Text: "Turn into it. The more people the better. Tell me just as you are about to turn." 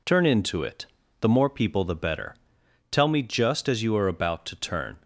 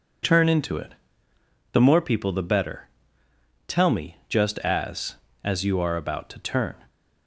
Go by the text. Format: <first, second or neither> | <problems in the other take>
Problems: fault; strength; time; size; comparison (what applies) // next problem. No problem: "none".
first | says "as" twice; at 5.4 s